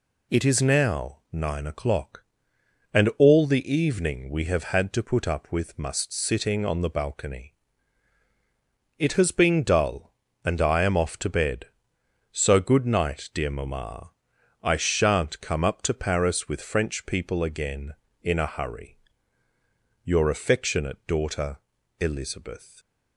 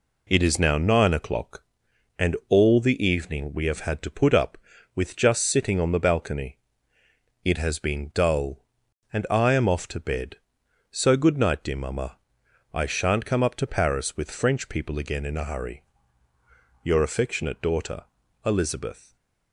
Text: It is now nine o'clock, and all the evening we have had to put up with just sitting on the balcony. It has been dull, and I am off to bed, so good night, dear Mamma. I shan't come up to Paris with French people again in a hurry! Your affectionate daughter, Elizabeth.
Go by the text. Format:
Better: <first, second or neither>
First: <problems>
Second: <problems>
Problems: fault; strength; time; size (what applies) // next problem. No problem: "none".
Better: second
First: says "must" for "just"; at 5.7 s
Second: none